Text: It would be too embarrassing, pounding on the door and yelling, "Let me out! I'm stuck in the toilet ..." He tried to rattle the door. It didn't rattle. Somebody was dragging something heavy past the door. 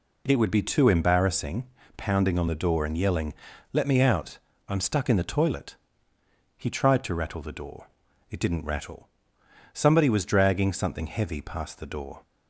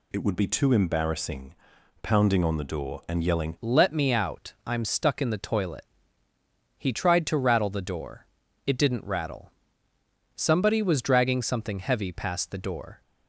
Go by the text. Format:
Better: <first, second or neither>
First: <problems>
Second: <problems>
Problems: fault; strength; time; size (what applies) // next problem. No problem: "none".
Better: first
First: none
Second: changes voice at "Let"; from 3.5 s on; 9.5 s long